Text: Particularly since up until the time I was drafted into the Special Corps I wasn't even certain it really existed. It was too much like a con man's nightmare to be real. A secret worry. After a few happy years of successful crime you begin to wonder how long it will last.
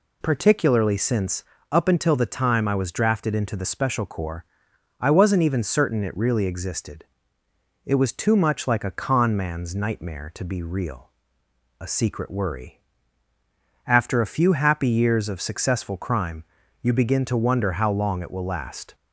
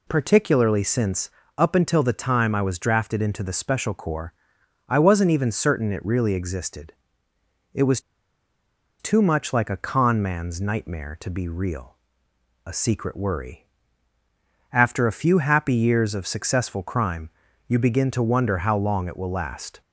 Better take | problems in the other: first | pauses between "since" and "up"; slight; at 1.2 s; 0.28 s long; slight in the first // pauses between "Corps" and "I"; noticeable; at 4.3 s; 0.54 s long; noticeable in the first // pauses between "was" and "too"; at 7.9 s; 1.0 s long // pauses between "crime" and "you"; at 17.2 s; 0.38 s long; also in the first

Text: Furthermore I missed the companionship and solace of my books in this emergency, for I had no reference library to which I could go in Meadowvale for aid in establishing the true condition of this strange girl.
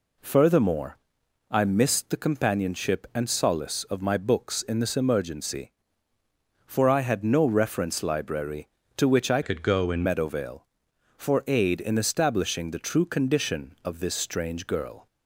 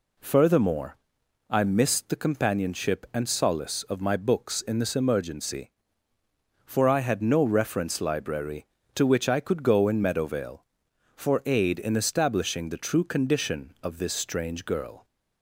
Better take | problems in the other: second | pauses between "Furthermore" and "I"; noticeable; at 0.9 s; 0.52 s long; noticeable in the second // changes voice from "could" to "in"; from 9.4 to 10.0 s; 0.6 s long

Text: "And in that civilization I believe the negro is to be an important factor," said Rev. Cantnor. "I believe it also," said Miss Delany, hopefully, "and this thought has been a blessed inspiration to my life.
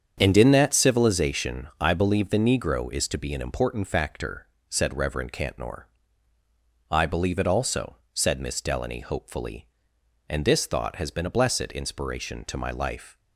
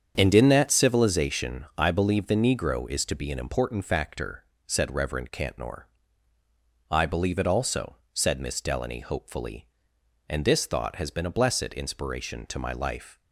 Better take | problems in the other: neither | starts louder than the rest; strong; the same in both

